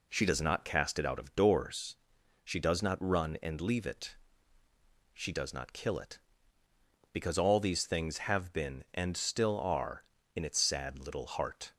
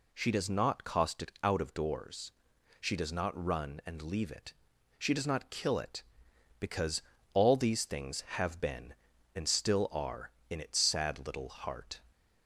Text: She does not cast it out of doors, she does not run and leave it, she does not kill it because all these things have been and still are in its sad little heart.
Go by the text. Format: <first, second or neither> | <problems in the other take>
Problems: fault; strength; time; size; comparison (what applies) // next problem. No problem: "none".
first | says "cost" for "cast"; at 0.8 s // pauses between "because" and "all"; slight; at 7.0 s; 0.32 s long